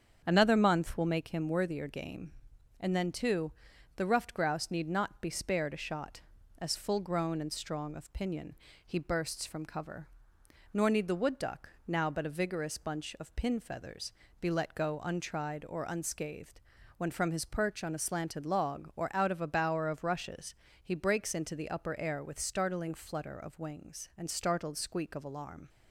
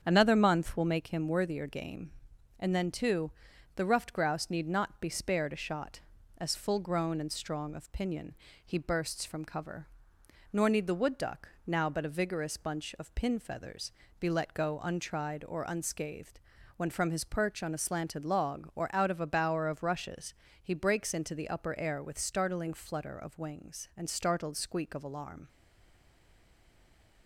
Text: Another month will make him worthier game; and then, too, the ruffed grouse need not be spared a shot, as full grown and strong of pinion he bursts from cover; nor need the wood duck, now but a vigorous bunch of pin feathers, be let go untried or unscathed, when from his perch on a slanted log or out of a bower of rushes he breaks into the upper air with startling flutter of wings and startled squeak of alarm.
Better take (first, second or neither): first